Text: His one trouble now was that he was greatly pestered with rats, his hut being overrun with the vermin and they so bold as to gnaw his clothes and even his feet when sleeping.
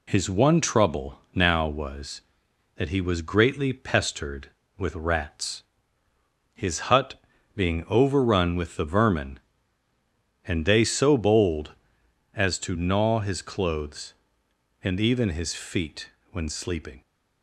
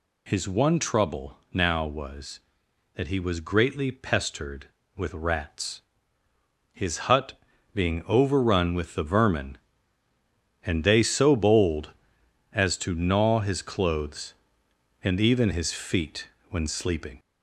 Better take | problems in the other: first | gets louder; slight; throughout; 3 dB // pauses between "trouble" and "now"; slight; at 1.3 s; 0.16 s long; slight in the first // pauses between "hut" and "being"; slight; at 7.3 s; 0.34 s long; slight in the first // pauses between "feet" and "when"; slight; at 16.2 s; 0.22 s long; slight in the first

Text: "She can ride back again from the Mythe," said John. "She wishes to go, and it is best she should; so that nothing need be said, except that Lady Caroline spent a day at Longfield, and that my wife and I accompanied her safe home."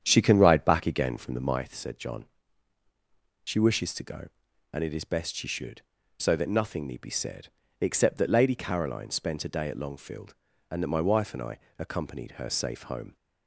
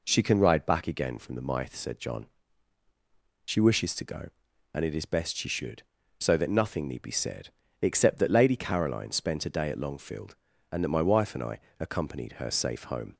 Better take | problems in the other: second | starts louder than the rest; strong; until 1.6 s; 8.5 dB // pauses between "I" and "accompanied"; slight; at 11.5 s; 0.18 s long; slight in the second

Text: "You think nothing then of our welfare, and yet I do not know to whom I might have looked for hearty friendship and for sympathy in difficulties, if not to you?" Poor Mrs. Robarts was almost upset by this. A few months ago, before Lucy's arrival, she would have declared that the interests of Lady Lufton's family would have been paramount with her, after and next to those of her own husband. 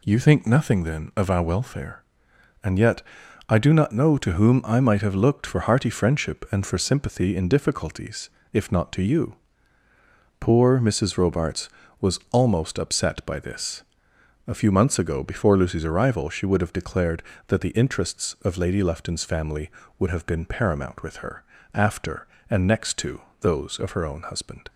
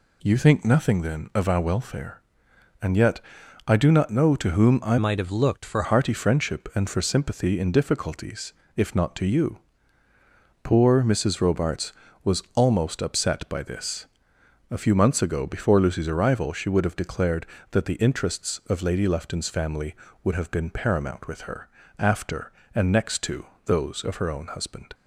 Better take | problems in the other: first | pauses between "yet" and "I"; noticeable; at 3.2 s; 0.46 s long; noticeable in the first // changes voice from "might" to "for"; from 4.9 to 5.8 s; 0.9 s long // pauses between "to" and "those"; slight; at 23.4 s; 0.22 s long; slight in the first

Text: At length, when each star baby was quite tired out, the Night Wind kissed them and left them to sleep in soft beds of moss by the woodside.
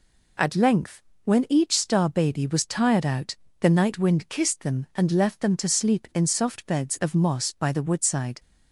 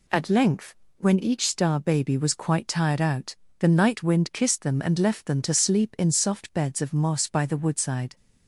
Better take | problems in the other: second | skips "quite"; at 2.6 s

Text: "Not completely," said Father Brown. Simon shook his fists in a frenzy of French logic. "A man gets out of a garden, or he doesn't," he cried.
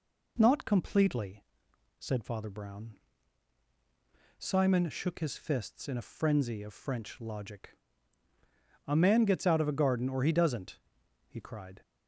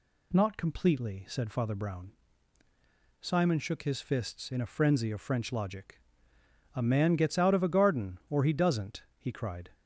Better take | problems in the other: neither | none

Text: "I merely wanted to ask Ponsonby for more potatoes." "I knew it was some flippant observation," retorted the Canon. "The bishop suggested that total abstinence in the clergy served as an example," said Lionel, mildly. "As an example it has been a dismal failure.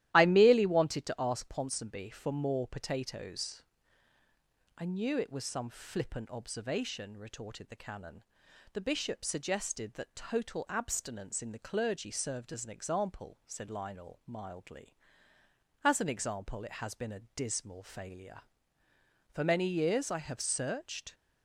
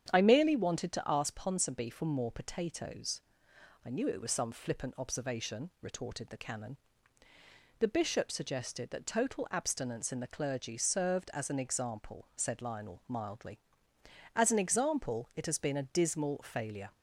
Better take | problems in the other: second | starts louder than the rest; strong; until 1.1 s; 14 dB; strong in the second // pauses between "a" and "dismal"; slight; at 17.1 s; 0.16 s long // goes on to say "For many years I have searched"; strong; from 19.3 s on; 1.8 s long

